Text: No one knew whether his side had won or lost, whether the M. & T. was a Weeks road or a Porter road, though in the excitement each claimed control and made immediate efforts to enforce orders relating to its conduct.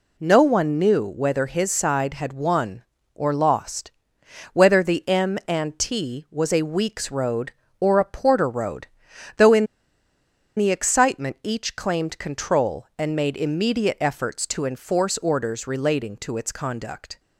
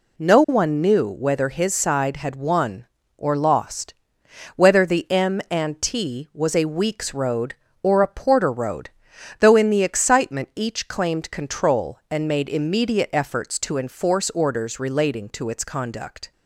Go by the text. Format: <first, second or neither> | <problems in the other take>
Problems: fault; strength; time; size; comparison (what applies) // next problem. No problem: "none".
second | pauses between "in" and "the"; noticeable; at 9.6 s; 0.91 s long